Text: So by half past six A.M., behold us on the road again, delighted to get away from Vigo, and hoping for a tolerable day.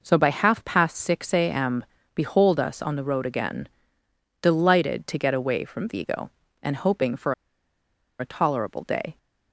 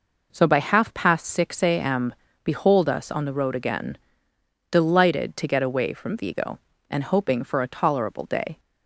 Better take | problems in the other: second | pauses between "for" and "a"; noticeable; at 7.3 s; 0.85 s long

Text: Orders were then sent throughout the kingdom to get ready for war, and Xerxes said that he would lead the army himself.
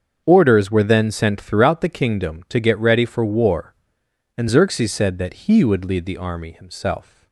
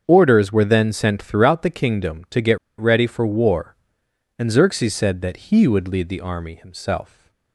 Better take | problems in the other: first | starts louder than the rest; until 1.0 s; 7 dB; also in the first // pauses between "get" and "ready"; slight; at 2.5 s; 0.22 s long

